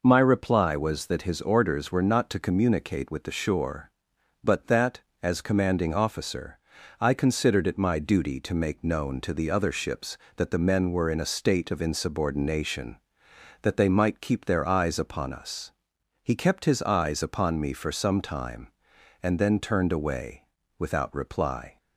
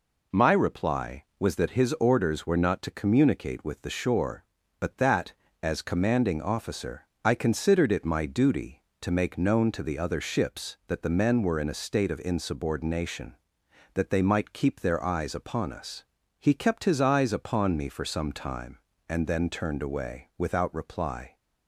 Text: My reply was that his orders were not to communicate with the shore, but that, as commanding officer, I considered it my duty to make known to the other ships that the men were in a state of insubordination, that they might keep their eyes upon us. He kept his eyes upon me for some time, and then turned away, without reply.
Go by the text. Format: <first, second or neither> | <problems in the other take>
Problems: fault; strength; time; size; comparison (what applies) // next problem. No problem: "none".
neither | none